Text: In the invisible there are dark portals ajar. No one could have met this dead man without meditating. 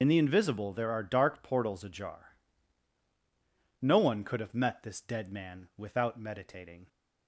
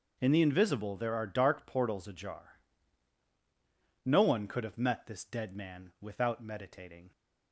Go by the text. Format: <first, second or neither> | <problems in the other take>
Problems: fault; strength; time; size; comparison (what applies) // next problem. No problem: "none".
second | loses the start of "In"; at 0.0 s; 50 ms // starts louder than the rest; noticeable; until 1.0 s; 6 dB; noticeable in the second